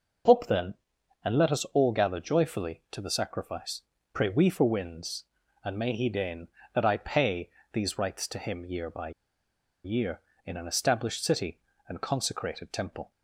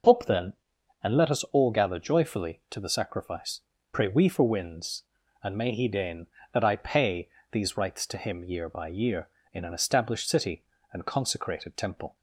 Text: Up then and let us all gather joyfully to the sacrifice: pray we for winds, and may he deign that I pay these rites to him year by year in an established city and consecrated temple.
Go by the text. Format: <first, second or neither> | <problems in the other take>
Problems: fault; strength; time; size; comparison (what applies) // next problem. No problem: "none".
second | pauses between "pay" and "these"; slight; at 7.4 s; 0.26 s long; slight in the second // pauses between "by" and "year"; noticeable; at 9.1 s; 0.74 s long